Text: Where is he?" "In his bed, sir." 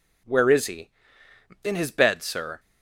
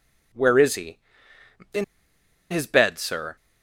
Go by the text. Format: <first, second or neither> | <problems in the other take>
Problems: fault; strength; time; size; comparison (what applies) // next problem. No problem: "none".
first | pauses between "In" and "his"; noticeable; at 1.8 s; 0.66 s long